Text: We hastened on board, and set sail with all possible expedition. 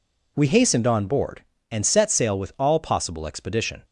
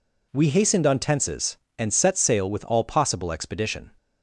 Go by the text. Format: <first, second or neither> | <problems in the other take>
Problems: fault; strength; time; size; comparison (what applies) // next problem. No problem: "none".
first | says "tenses" for "board"; at 0.9 s